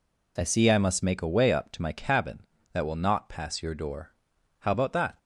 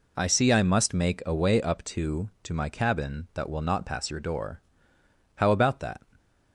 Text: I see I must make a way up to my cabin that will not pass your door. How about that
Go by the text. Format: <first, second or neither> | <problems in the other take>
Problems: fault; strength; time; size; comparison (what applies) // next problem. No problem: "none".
first | says "to" twice; at 2.4 s